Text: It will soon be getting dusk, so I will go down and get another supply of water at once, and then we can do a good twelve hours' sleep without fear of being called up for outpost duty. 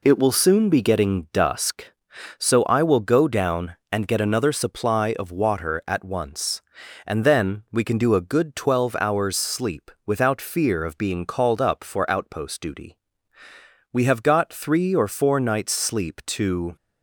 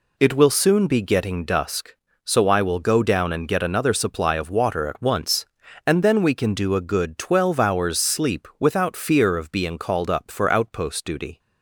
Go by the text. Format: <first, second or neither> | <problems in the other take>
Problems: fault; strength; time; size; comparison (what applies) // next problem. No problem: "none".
second | pauses between "sleep" and "without"; slight; at 9.8 s; 0.16 s long // goes on to say "We have got three or four nights sleep to"; strong; from 13.9 s on; 2.8 s long